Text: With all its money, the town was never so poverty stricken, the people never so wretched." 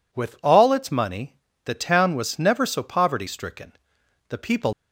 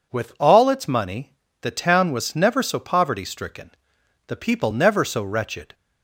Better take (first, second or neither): second